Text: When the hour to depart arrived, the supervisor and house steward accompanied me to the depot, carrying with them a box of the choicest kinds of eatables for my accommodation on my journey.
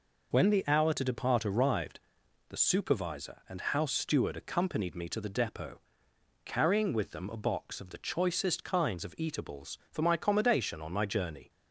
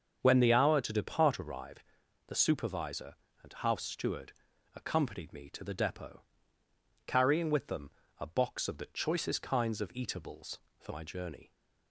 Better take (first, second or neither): first